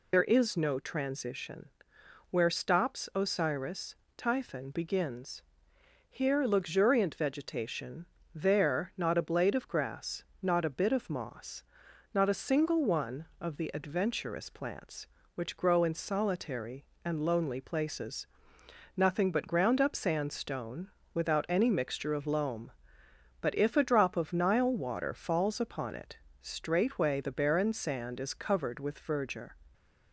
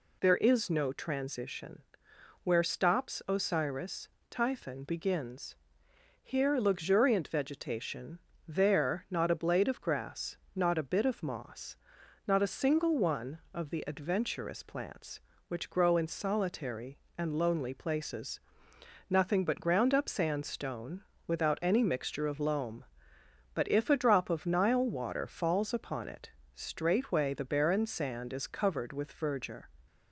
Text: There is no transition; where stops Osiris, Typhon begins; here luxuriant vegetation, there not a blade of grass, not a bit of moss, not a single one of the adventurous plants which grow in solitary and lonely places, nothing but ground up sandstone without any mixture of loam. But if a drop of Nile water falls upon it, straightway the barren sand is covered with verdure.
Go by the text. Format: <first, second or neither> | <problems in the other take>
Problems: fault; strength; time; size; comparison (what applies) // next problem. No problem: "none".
second | loses the start of "There"; at 0.1 s; 55 ms // pauses between "sandstone" and "without"; slight; at 20.8 s; 0.24 s long; slight in the second